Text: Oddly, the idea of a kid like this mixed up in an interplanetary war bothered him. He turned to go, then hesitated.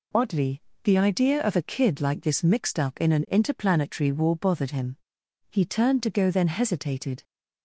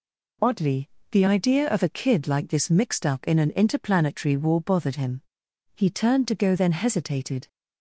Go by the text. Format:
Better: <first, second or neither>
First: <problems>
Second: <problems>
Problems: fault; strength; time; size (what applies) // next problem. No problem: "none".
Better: neither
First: none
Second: none